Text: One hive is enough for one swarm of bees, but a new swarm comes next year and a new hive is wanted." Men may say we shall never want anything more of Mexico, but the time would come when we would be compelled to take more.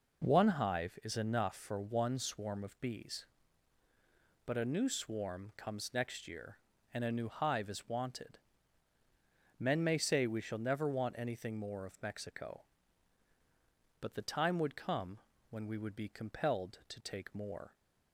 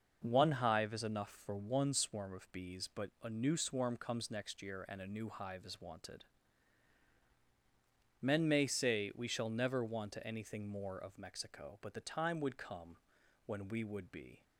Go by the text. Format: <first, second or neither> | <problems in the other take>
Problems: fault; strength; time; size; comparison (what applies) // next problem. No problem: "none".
first | starts louder than the rest; noticeable; until 1.2 s; 6 dB // pauses between "come" and "when"; noticeable; at 12.9 s; 0.50 s long; slight in the first // stops before "compelled to take more"; at 14.4 s